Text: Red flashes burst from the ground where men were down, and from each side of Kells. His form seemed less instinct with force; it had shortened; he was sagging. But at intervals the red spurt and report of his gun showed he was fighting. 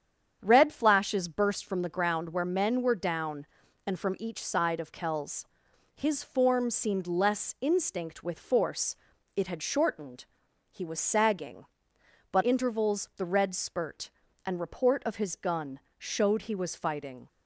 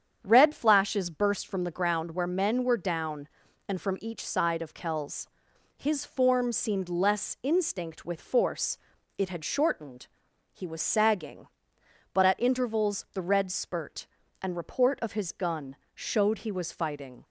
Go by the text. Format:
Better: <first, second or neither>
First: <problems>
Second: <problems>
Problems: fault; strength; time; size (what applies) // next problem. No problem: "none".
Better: second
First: starts louder than the rest; strong; until 1.4 s; 8.5 dB // skips "at"; at 12.4 s // pauses between "gun" and "showed"; slight; at 15.7 s; 0.18 s long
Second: starts louder than the rest; strong; until 1.2 s; 8.5 dB // pauses between "gun" and "showed"; slight; at 15.7 s; 0.18 s long